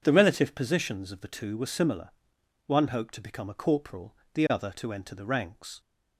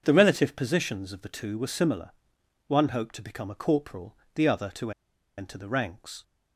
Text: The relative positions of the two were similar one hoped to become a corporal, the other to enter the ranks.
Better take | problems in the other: first | pauses between "similar" and "one"; noticeable; at 2.1 s; 0.56 s long; noticeable in the first // pauses between "to" and "enter"; noticeable; at 4.9 s; 0.47 s long

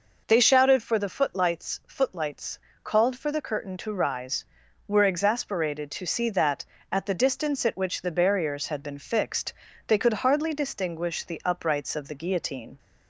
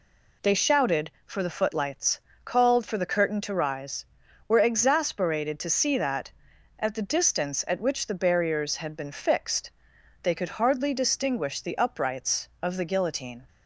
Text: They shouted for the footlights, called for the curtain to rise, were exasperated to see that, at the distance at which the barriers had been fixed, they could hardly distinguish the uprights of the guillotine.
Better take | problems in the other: second | says "footlights" twice; at 1.8 s

